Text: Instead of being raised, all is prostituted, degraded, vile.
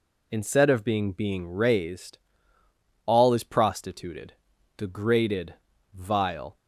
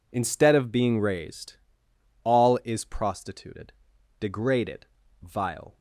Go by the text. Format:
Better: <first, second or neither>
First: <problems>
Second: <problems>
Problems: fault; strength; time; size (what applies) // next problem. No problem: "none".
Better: second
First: says "being" twice; at 1.1 s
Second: none